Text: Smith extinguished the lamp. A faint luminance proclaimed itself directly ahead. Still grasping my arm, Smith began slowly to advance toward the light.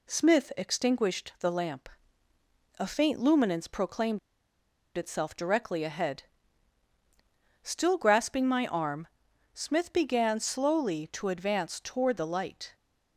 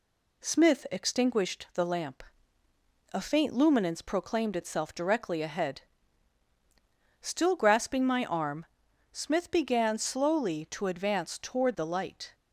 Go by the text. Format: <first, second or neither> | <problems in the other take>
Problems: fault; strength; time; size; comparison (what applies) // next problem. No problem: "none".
second | pauses between "proclaimed" and "itself"; noticeable; at 4.1 s; 0.77 s long